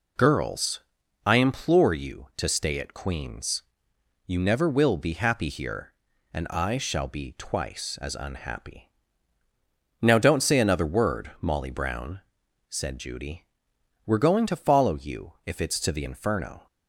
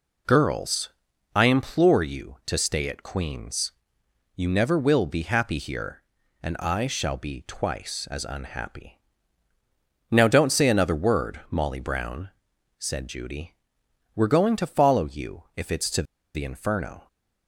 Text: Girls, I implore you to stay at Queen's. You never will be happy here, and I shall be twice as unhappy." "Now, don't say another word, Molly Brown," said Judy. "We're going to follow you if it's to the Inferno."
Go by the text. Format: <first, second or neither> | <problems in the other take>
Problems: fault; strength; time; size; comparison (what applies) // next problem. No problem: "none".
first | pauses between "to" and "the"; slight; at 16.0 s; 0.30 s long